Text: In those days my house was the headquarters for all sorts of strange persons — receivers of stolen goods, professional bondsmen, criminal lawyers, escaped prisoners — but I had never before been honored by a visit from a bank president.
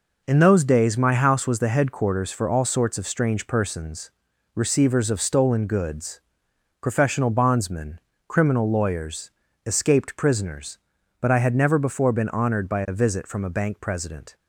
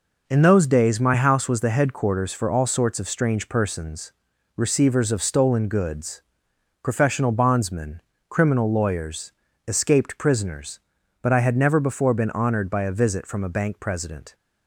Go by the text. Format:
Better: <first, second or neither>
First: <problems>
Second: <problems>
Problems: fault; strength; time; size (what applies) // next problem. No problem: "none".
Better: neither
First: none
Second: none